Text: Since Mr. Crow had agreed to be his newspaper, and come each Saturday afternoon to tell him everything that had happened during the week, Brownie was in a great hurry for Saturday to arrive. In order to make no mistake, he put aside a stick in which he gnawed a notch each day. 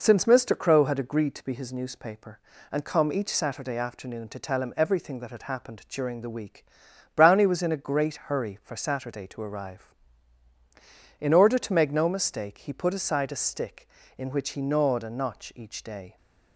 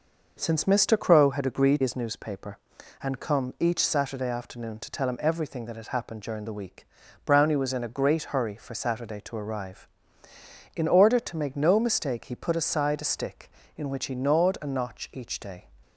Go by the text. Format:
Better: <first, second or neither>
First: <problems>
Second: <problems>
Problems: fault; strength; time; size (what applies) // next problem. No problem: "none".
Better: first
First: none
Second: skips "to be"; at 1.8 s